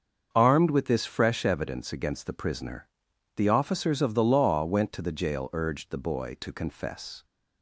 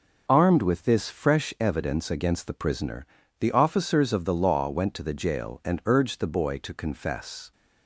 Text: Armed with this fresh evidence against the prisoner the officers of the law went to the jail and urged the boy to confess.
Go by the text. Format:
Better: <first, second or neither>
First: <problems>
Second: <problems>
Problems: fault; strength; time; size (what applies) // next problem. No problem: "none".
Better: second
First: starts louder than the rest; until 1.3 s; 6.5 dB // pauses between "prisoner" and "the"; noticeable; at 2.8 s; 0.48 s long // skips "and"; at 5.4 s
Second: pauses between "prisoner" and "the"; slight; at 3.0 s; 0.32 s long